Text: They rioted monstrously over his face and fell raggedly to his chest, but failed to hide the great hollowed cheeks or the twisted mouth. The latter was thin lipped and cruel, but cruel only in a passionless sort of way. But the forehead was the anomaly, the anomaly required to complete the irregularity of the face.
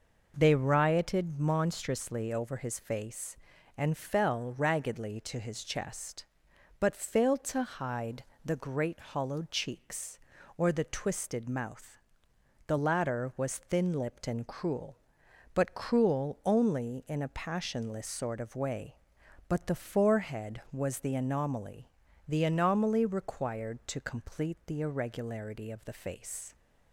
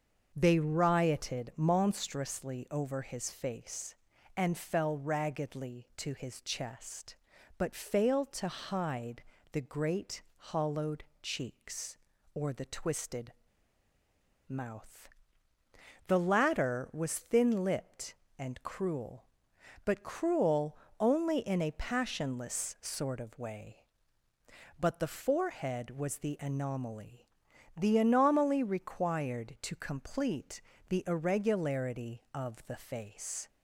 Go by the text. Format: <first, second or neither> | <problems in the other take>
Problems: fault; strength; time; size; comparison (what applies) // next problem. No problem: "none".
first | starts louder than the rest; until 1.3 s; 6.5 dB // pauses between "hide" and "the"; slight; at 9.2 s; 0.30 s long; slight in the first // pauses between "hollowed" and "cheeks"; slight; at 11.0 s; 0.18 s long // pauses between "twisted" and "mouth"; at 13.3 s; 1.1 s long // pauses between "cruel" and "only"; slight; at 20.7 s; 0.24 s long // pauses between "complete" and "the"; slight; at 30.5 s; 0.30 s long